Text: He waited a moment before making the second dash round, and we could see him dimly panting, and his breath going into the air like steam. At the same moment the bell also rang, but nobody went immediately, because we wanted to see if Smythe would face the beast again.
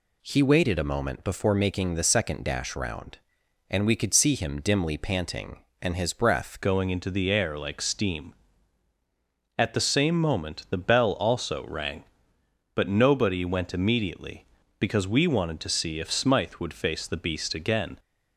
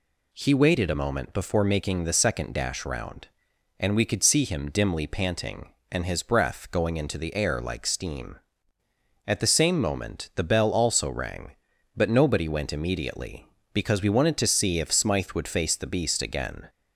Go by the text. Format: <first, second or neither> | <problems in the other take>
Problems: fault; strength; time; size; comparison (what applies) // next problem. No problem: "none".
second | changes voice at "going"; from 6.6 s on; 11.3 s long